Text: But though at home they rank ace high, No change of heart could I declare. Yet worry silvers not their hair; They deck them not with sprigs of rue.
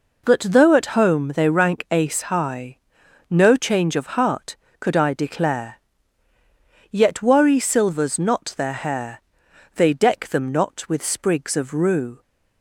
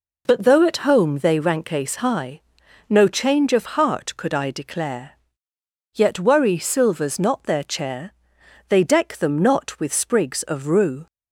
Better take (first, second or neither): first